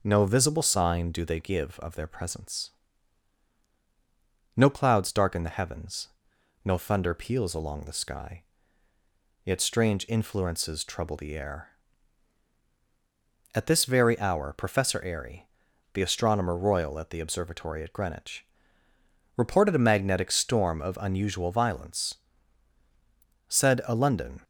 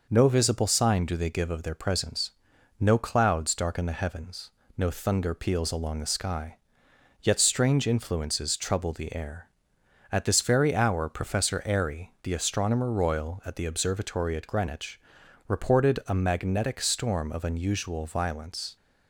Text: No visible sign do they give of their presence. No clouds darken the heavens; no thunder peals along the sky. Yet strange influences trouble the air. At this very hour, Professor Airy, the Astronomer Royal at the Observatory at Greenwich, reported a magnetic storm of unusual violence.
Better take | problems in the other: second | goes on to say "Said a London"; noticeable; from 23.4 s on; 0.94 s long

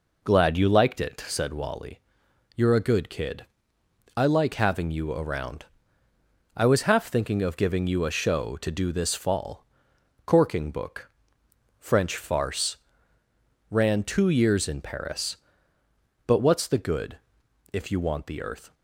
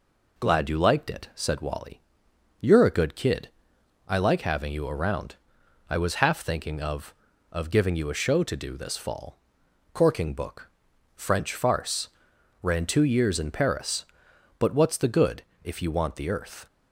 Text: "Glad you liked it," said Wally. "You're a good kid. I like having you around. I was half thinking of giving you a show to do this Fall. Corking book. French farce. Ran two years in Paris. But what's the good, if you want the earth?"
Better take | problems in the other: first | says "of" twice; at 7.5 s

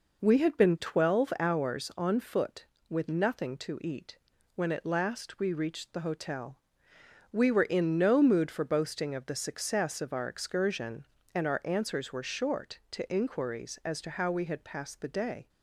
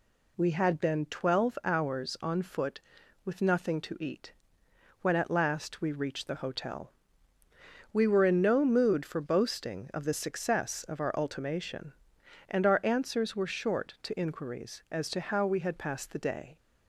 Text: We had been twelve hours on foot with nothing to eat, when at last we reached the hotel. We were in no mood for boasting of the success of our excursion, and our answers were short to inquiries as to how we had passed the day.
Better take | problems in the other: first | says "ultimation" for "excursion"; at 11.1 s

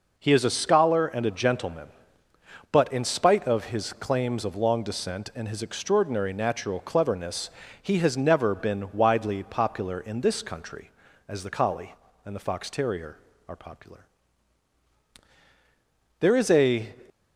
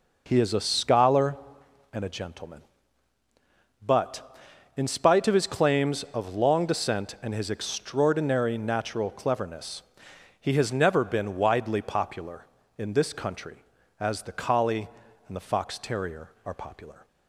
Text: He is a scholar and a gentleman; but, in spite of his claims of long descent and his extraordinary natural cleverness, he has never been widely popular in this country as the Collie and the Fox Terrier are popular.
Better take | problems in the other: second | goes on to say "There is a"; noticeable; from 16.2 s on; 0.74 s long

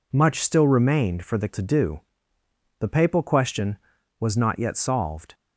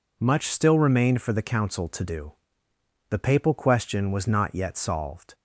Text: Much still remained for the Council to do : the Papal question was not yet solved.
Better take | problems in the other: second | skips "Council"; at 1.4 s

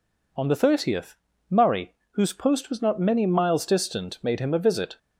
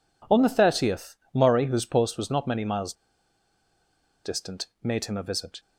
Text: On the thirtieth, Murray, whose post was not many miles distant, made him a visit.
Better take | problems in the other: first | pauses between "miles" and "distant"; strong; at 2.9 s; 1.3 s long

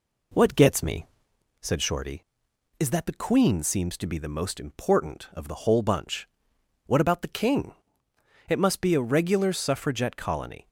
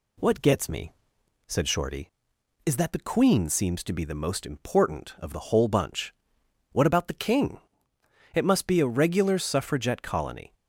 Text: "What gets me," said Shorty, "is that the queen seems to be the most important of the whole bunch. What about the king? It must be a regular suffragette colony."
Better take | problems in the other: second | starts louder than the rest; until 1.3 s; 3.5 dB

